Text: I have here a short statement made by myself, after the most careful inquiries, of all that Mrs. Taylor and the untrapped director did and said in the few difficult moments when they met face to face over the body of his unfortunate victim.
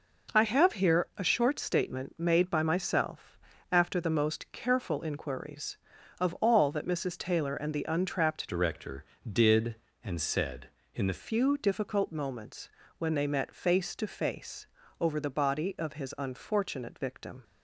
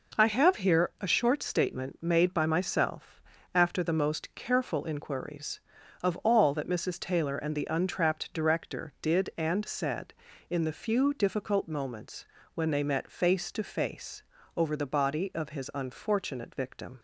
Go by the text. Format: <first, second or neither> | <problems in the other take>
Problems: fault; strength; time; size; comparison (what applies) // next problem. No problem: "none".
second | changes voice from "director" to "the"; from 8.4 to 11.2 s; 2.8 s long // pauses between "moments" and "when"; slight; at 12.6 s; 0.30 s long; slight in the second // pauses between "face" and "over"; slight; at 14.6 s; 0.36 s long; slight in the second